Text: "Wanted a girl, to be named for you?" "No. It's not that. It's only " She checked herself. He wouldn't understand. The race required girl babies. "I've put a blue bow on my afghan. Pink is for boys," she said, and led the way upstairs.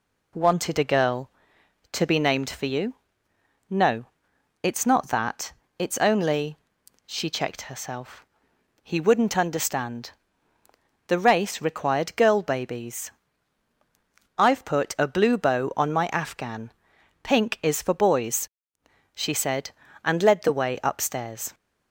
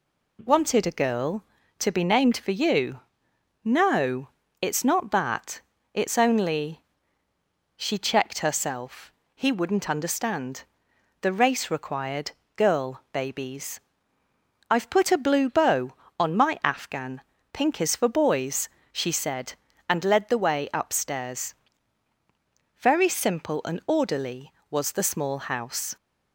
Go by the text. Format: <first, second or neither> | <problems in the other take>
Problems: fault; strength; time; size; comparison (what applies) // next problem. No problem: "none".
first | pauses between "required" and "girl"; slight; at 12.3 s; 0.24 s long // goes on to say "Very simple and orderly was the small house"; strong; from 22.7 s on; 3.1 s long